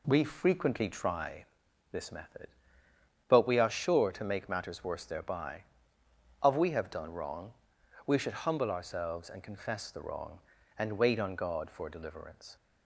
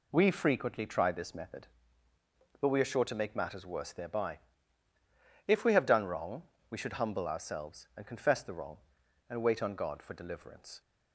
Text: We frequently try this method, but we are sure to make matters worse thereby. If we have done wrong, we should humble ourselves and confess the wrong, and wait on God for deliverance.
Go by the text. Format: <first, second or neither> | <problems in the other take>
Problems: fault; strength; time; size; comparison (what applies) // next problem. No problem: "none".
second | pauses between "try" and "this"; noticeable; at 1.4 s; 0.46 s long // says "Of" for "If"; at 6.4 s